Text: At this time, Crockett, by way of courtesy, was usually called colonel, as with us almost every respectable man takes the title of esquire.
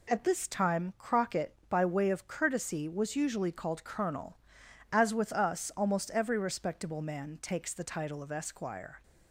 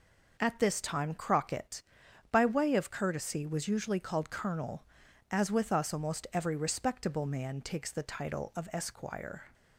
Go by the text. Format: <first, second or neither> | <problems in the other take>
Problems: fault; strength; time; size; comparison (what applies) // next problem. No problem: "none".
neither | none